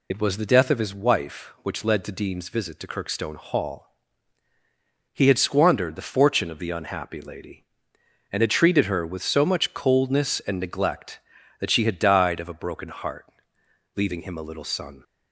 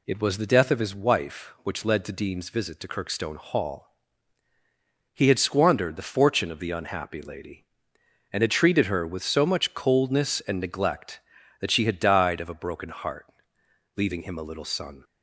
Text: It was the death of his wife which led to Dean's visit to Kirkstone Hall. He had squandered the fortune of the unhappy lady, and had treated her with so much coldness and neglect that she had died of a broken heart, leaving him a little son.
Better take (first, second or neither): second